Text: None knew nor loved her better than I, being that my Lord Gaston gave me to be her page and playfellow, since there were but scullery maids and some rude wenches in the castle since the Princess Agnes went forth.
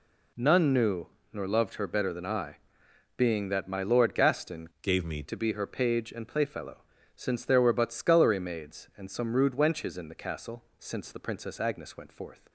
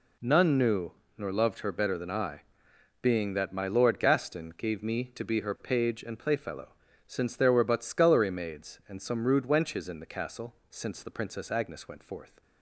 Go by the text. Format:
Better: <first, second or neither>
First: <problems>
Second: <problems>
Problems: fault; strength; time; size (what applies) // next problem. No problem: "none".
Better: second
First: pauses between "knew" and "nor"; slight; at 1.0 s; 0.24 s long // changes voice from "gave" to "me"; from 4.8 to 5.2 s; 0.4 s long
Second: pauses between "knew" and "nor"; slight; at 0.9 s; 0.24 s long